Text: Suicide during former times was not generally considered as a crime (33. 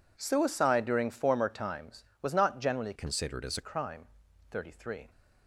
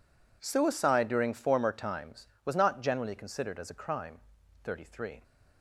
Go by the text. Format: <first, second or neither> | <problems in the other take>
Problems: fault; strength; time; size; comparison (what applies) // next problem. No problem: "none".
second | changes voice from "considered" to "a"; from 2.9 to 3.6 s; 0.7 s long